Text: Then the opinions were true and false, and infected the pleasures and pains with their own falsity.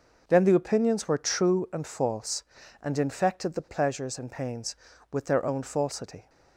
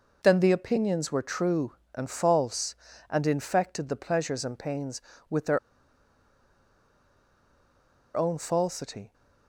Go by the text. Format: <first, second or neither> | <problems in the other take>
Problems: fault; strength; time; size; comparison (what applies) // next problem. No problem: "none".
first | pauses between "their" and "own"; strong; at 5.5 s; 2.5 s long